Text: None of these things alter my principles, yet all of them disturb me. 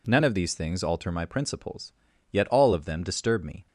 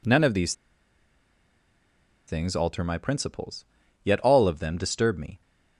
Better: first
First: none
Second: pauses between "these" and "things"; strong; at 0.5 s; 1.7 s long

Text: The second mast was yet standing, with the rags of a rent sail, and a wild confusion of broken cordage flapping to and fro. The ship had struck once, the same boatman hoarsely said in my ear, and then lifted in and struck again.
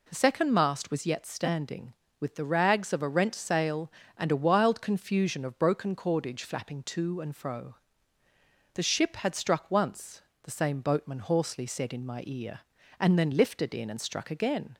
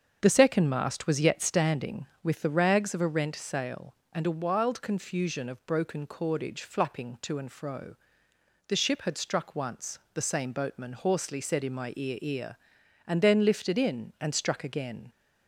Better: first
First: none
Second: starts louder than the rest; until 1.2 s; 7 dB // says "ear" twice; at 12.2 s

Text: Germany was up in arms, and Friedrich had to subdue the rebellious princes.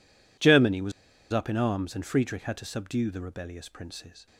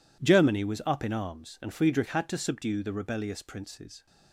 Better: second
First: pauses between "was" and "up"; at 0.9 s; 0.40 s long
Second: none

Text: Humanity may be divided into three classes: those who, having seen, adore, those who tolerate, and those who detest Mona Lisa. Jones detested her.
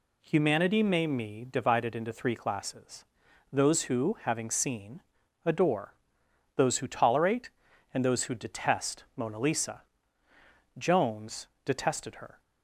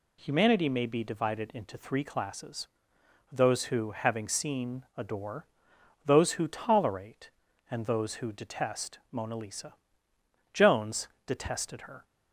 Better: second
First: says "me" for "be"; at 1.0 s // pauses between "Jones" and "detested"; slight; at 11.4 s; 0.18 s long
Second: pauses between "Jones" and "detested"; slight; at 11.0 s; 0.18 s long

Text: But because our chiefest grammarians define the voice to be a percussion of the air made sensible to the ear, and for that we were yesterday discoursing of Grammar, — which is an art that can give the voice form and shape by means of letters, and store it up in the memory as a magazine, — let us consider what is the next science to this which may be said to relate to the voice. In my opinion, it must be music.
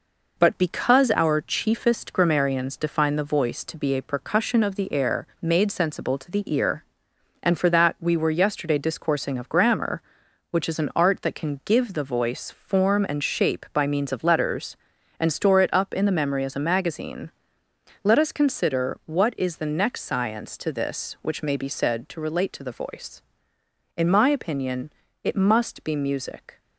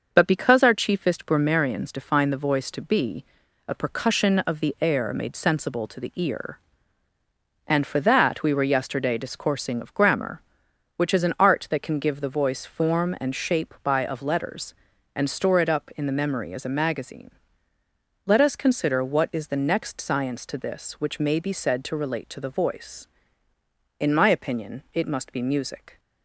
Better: first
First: none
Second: starts louder than the rest; until 1.1 s; 6 dB // pauses between "be" and "a"; at 3.2 s; 0.42 s long // skips "means"; at 14.0 s

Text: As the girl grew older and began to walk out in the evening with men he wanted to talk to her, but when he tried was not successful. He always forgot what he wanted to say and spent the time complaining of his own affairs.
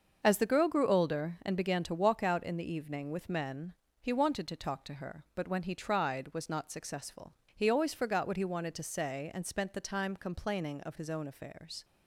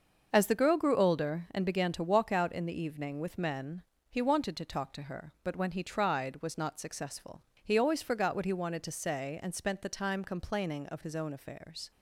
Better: neither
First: starts louder than the rest; until 1.2 s; 6.5 dB // pauses between "men" and "he"; slight; at 3.7 s; 0.26 s long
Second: starts louder than the rest; until 1.3 s; 6.5 dB // pauses between "men" and "he"; slight; at 3.8 s; 0.26 s long

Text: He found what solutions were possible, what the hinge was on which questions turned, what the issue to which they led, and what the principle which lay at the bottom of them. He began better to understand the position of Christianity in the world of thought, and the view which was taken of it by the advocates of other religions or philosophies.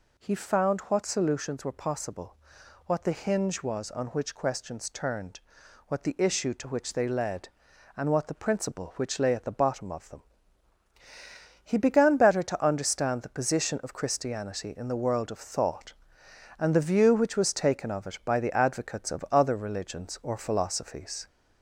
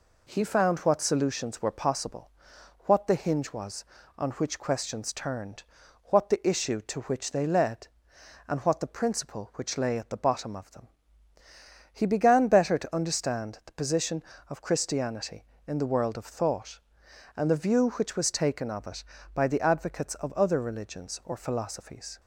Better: second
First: gets louder; slight; throughout; 3 dB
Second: none

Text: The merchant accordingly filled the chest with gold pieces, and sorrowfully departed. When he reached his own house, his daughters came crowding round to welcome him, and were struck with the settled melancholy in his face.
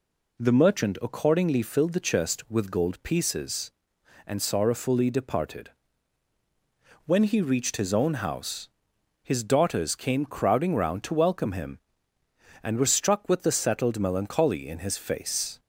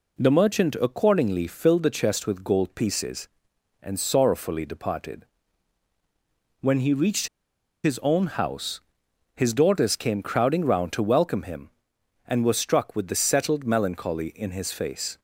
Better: first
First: none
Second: pauses between "reached" and "his"; noticeable; at 7.2 s; 0.56 s long

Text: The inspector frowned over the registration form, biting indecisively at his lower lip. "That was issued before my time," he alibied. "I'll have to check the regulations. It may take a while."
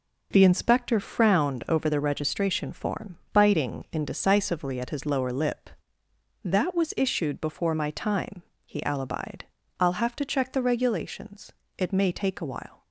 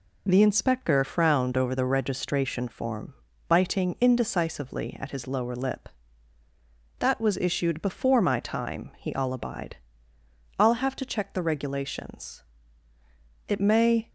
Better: first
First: none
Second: stops before "take a while"; at 14.0 s

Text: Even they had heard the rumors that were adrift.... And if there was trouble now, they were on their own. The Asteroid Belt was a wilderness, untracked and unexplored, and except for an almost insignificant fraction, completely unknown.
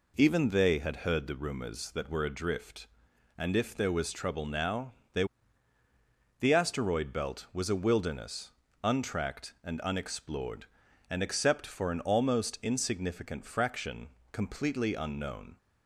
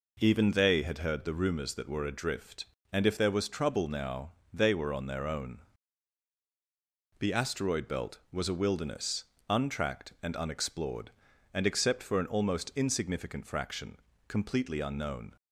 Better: second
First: skips "were on their own"; at 5.8 s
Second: none

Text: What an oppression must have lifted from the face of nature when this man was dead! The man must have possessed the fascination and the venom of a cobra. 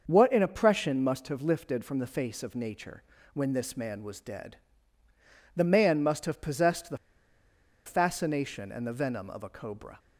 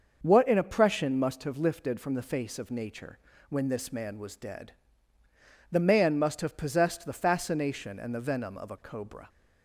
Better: second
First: starts louder than the rest; until 1.0 s; 6.5 dB // pauses between "nature" and "when"; slight; at 3.0 s; 0.32 s long // pauses between "the" and "fascination"; noticeable; at 6.9 s; 0.89 s long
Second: starts louder than the rest; until 1.2 s; 6.5 dB // pauses between "nature" and "when"; slight; at 3.1 s; 0.32 s long

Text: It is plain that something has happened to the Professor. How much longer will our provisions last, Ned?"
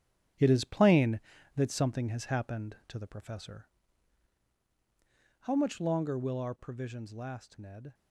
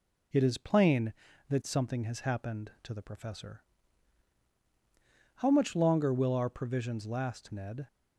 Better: second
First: gets quieter; strong; throughout; 9 dB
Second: none

